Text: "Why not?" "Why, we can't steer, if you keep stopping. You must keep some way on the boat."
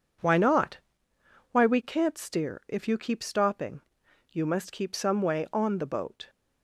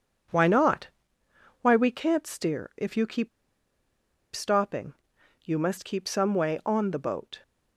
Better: first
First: none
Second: pauses between "keep" and "stopping"; at 3.2 s; 1.0 s long

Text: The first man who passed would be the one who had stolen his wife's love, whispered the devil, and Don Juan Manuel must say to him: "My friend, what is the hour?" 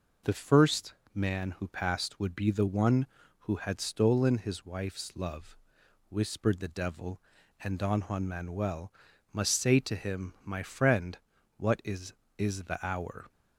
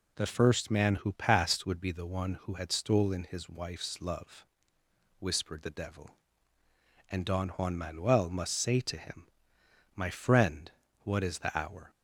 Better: second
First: pauses between "first" and "man"; slight; at 0.9 s; 0.20 s long // pauses between "Manuel" and "must"; at 8.9 s; 0.42 s long // says "is" twice; at 12.3 s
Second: none

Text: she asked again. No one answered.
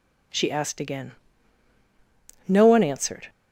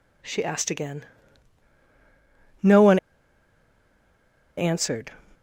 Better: first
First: none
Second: pauses between "one" and "answered"; strong; at 2.9 s; 1.6 s long

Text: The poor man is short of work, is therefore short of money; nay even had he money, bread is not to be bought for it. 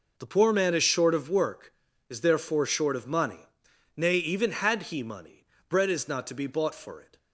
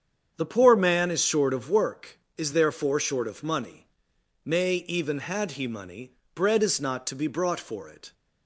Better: first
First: none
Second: starts louder than the rest; strong; until 1.3 s; 8 dB // says "brought" for "bought"; at 7.2 s

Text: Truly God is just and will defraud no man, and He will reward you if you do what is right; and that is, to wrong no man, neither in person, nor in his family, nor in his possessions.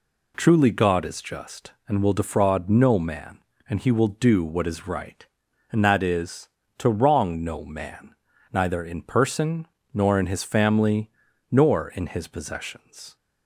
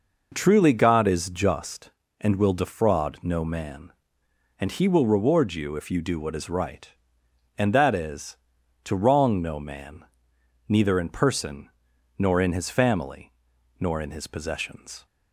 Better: second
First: skips "reward you if you"; at 4.0 s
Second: none

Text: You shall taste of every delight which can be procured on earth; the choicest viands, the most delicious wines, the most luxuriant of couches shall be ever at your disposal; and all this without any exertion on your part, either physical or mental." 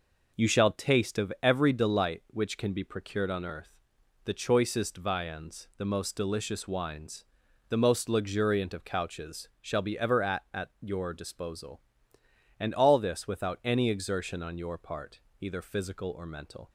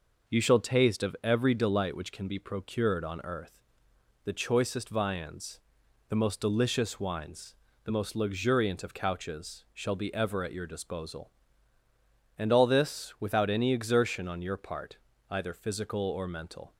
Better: second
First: says "at" twice; at 10.5 s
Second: none

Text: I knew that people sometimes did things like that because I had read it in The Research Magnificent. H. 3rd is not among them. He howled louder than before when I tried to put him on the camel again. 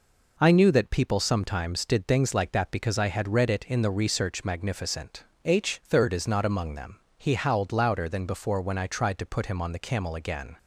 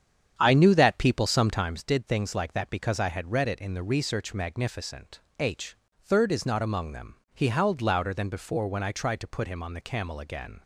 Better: first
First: none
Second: starts louder than the rest; strong; until 1.9 s; 8.5 dB

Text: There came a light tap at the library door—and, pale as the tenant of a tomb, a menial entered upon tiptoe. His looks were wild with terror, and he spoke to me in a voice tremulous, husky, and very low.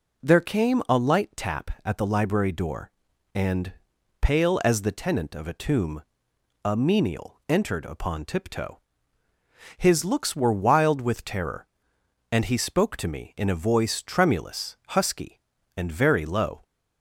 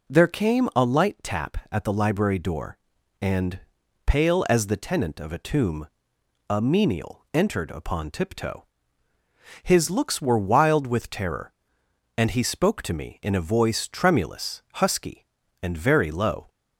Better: neither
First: none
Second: none

